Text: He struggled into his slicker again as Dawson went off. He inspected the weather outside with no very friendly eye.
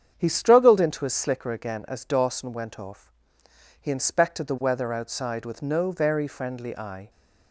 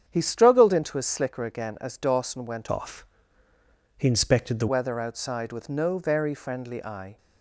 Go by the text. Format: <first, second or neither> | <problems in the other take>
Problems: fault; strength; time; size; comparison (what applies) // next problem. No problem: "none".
first | starts louder than the rest; strong; until 1.0 s; 8 dB; strong in the first // changes voice from "off" to "the"; from 2.7 to 4.6 s; 1.9 s long